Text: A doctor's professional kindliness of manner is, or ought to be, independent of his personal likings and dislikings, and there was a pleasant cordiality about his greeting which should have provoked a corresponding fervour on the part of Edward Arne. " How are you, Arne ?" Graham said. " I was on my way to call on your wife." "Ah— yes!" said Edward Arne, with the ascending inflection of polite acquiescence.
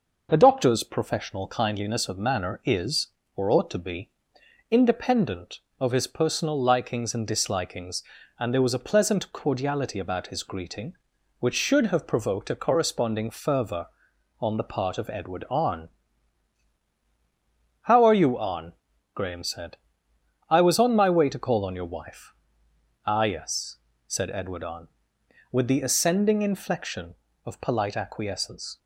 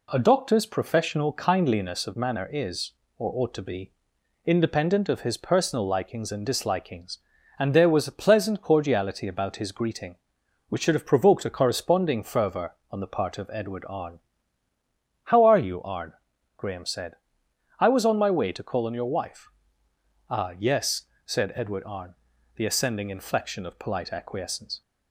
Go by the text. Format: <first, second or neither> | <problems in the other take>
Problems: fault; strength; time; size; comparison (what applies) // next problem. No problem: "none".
first | skips "with"; at 22.3 s